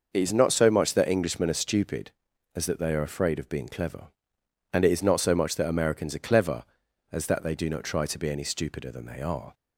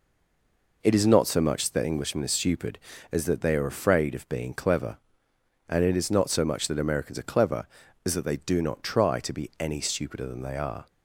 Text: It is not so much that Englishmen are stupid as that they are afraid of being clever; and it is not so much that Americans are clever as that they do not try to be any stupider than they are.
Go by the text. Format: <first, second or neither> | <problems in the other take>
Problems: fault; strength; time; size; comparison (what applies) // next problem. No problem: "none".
first | stays silent before the first word; slight; until 0.8 s; 0.8 s long